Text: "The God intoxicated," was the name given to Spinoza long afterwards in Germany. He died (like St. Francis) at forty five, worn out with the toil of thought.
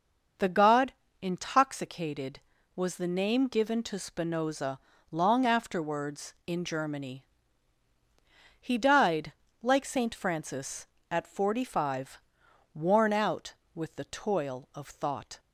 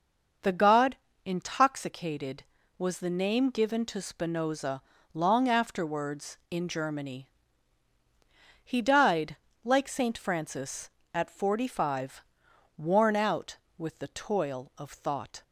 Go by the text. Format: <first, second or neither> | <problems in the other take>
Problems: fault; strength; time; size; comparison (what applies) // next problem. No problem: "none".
neither | starts louder than the rest; the same in both // pauses between "God" and "intoxicated"; slight; the same in both // pauses between "Spinoza" and "long"; slight; the same in both